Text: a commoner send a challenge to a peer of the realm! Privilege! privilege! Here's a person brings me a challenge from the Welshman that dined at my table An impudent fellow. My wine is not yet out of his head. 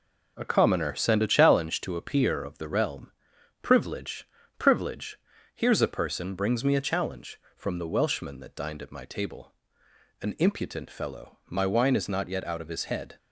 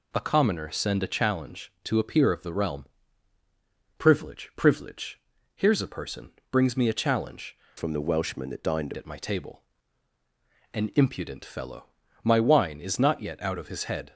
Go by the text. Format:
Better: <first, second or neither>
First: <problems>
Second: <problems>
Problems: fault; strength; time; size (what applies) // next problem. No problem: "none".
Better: first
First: pauses between "table" and "An"; noticeable; at 9.5 s; 0.68 s long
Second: pauses between "person" and "brings"; slight; at 6.3 s; 0.18 s long // changes voice from "from" to "dined"; from 7.7 to 8.9 s; 1.2 s long // pauses between "table" and "An"; at 9.6 s; 1.1 s long